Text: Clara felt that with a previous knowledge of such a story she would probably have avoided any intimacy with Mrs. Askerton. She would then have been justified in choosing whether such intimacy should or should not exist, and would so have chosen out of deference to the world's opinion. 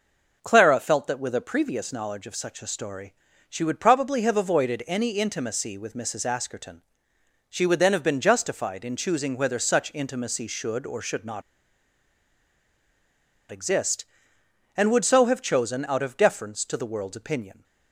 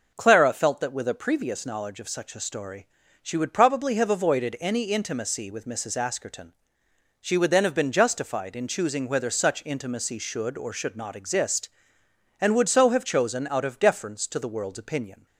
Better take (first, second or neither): second